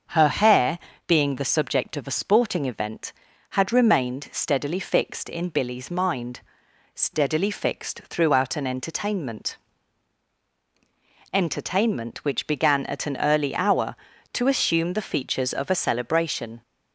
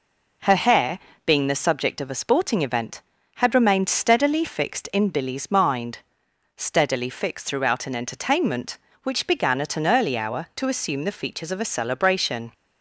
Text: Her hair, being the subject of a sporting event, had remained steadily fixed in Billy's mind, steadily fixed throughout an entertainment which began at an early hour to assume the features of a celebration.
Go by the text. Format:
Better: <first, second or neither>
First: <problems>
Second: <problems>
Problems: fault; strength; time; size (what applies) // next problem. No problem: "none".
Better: second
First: starts louder than the rest; until 1.3 s; 6.5 dB // says "entertainment" twice; at 11.3 s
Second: none